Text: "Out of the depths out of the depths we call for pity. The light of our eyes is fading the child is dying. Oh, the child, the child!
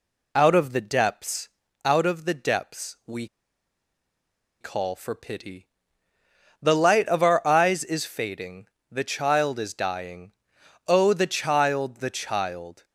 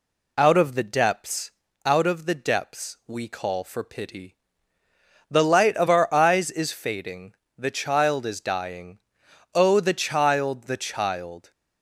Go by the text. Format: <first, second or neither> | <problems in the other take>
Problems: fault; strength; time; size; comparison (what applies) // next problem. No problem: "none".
second | pauses between "depths" and "out"; slight; at 1.4 s; 0.36 s long; slight in the second // pauses between "we" and "call"; strong; at 3.2 s; 1.3 s long // pauses between "fading" and "the"; slight; at 8.6 s; 0.24 s long; slight in the second